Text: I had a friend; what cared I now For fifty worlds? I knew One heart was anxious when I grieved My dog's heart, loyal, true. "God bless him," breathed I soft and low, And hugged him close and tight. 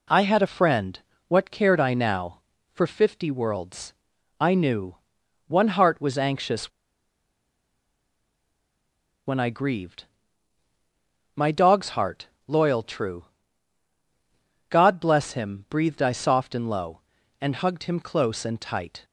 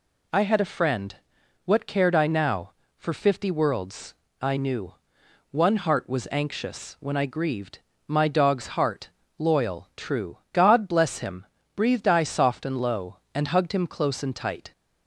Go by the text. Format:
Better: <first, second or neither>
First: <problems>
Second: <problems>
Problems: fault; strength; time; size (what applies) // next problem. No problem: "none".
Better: second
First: pauses between "knew" and "One"; noticeable; at 4.9 s; 0.54 s long // pauses between "anxious" and "when"; strong; at 6.7 s; 2.5 s long // pauses between "grieved" and "My"; strong; at 10.0 s; 1.3 s long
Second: pauses between "knew" and "One"; noticeable; at 4.9 s; 0.60 s long // pauses between "grieved" and "My"; slight; at 7.7 s; 0.30 s long